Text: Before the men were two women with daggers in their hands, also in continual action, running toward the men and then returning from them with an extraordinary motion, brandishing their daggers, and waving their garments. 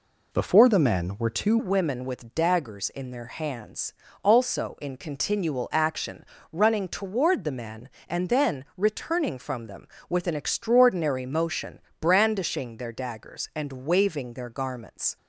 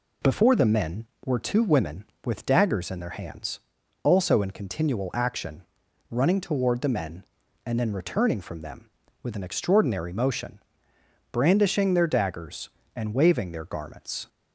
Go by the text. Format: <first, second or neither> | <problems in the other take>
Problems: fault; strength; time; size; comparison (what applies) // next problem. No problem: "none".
second | changes voice at "women"; from 1.5 s on; 13.6 s long